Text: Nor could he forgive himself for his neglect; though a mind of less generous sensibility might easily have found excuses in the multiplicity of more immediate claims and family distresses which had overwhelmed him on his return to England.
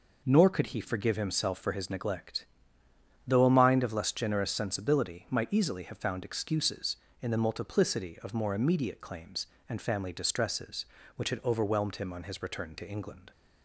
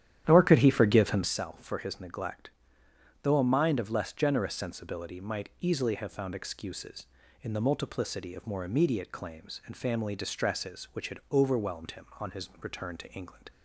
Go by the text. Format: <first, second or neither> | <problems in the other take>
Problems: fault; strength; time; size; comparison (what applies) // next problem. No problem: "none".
first | starts louder than the rest; strong; until 1.3 s; 11 dB